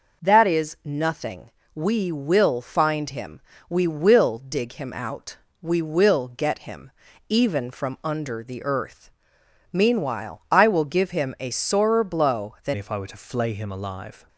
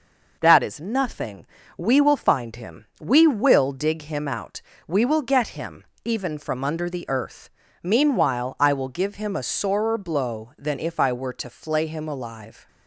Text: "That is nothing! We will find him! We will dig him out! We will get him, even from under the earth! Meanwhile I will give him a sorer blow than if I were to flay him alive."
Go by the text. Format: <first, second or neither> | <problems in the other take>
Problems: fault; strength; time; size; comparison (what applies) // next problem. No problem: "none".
second | changes voice at "if"; from 12.7 s on; 1.5 s long